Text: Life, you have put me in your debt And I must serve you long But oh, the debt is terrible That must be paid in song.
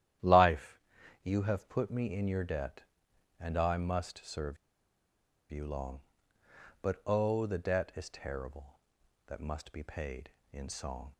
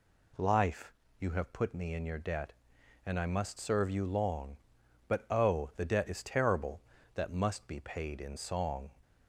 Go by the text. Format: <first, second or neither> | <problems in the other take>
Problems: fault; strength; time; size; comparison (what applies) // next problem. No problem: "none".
second | starts louder than the rest; strong; until 1.6 s; 11.5 dB // pauses between "serve" and "you"; noticeable; at 4.5 s; 0.93 s long